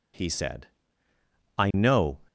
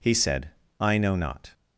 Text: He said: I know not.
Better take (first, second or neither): second